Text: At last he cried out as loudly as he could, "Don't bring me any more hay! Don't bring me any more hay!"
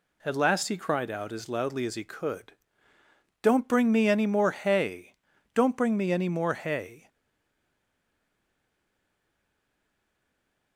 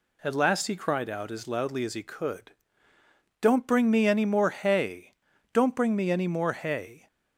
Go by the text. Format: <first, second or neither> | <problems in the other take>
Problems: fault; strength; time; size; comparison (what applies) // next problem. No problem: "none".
second | stays silent after the last word; strong; from 7.0 s on; 3.7 s long